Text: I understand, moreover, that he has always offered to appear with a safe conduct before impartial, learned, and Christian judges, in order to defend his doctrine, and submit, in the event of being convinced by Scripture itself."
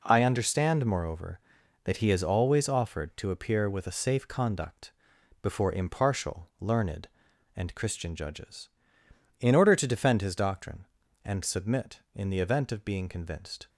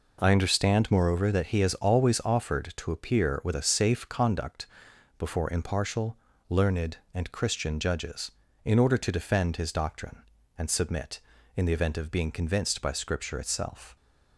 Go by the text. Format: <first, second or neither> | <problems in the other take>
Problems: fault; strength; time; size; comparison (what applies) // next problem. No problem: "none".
second | pauses between "conduct" and "before"; noticeable; at 4.9 s; 0.52 s long; noticeable in the second // stops before "by Scripture itself"; at 13.6 s